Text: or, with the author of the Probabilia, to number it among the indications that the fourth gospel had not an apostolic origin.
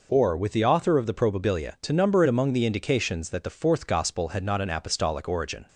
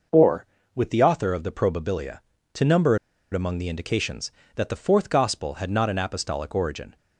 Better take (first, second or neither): first